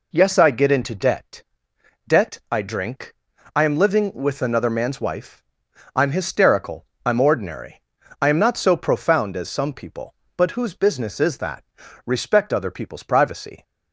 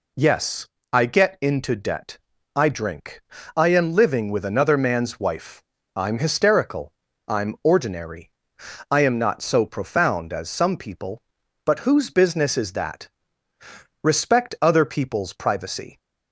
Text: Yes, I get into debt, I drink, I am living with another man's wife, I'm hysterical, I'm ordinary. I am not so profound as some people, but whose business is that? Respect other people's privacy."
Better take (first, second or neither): second